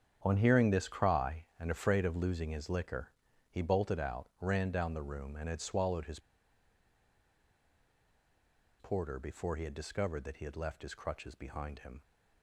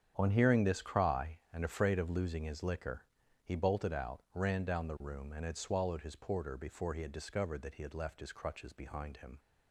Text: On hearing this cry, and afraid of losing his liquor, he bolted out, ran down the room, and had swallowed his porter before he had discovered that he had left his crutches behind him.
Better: second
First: starts louder than the rest; strong; until 1.2 s; 8.5 dB // pauses between "his" and "porter"; strong; at 6.1 s; 2.5 s long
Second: starts louder than the rest; strong; until 1.1 s; 8.5 dB

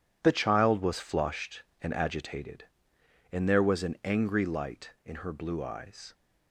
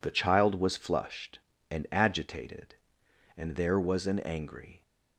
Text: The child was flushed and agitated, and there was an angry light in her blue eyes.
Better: first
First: none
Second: stops before "light in her blue eyes"; at 4.8 s

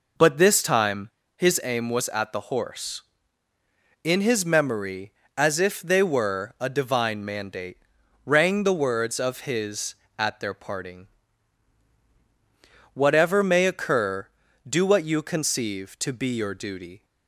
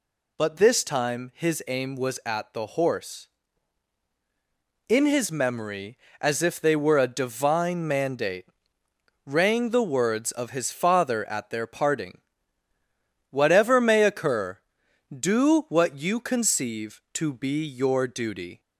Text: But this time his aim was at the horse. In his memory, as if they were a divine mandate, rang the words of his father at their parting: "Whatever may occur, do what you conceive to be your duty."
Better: second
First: pauses between "time" and "his"; slight; at 1.0 s; 0.26 s long // skips "father"; at 10.0 s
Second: none

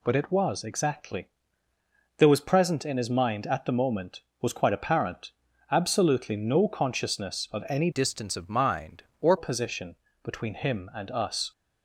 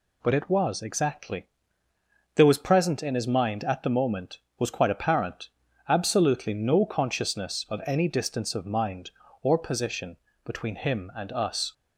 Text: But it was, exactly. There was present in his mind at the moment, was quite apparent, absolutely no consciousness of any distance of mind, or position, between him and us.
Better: second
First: changes voice from "distance" to "or"; from 7.9 to 9.3 s; 1.4 s long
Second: none

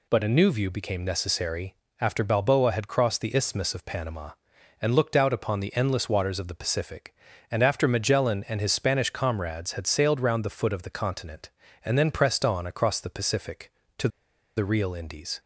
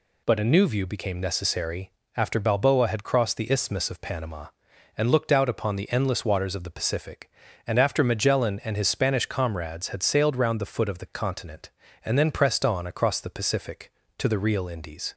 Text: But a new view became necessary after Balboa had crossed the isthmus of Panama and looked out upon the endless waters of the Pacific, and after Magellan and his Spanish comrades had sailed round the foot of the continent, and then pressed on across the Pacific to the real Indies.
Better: second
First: pauses between "necessary" and "after"; slight; at 1.7 s; 0.24 s long // pauses between "to" and "the"; noticeable; at 14.0 s; 0.49 s long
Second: pauses between "necessary" and "after"; slight; at 1.9 s; 0.24 s long

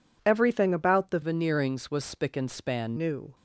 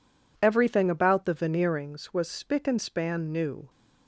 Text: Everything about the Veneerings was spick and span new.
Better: second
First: changes voice from "Veneerings" to "span"; from 1.2 to 2.9 s; 1.7 s long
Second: none

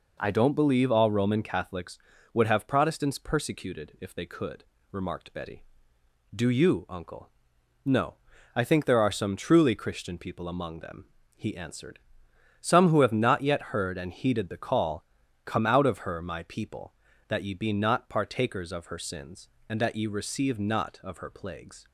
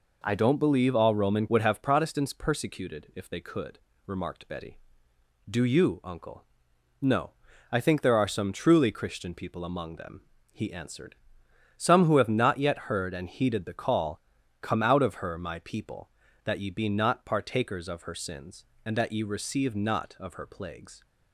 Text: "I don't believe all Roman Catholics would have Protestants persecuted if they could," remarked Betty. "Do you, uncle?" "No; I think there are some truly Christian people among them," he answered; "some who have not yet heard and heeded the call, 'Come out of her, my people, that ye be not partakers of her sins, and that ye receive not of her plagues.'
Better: first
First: none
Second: skips "Catholics"; at 1.4 s

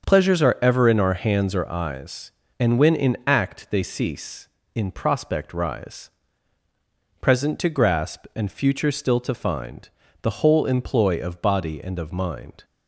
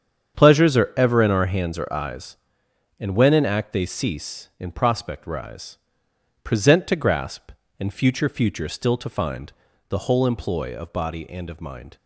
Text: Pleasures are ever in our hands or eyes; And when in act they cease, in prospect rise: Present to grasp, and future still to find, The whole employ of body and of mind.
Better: first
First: starts louder than the rest; until 1.0 s; 7 dB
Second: starts louder than the rest; strong; until 1.4 s; 8 dB // says "future" twice; at 8.2 s

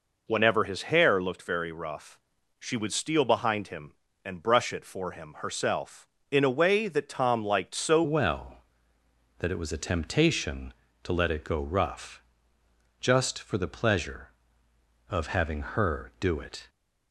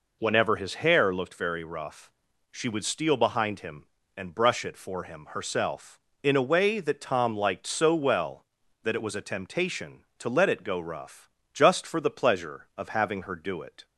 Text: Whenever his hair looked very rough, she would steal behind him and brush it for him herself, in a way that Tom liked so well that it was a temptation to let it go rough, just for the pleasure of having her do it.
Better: second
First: changes voice at "well"; from 8.0 s on; 8.6 s long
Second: none

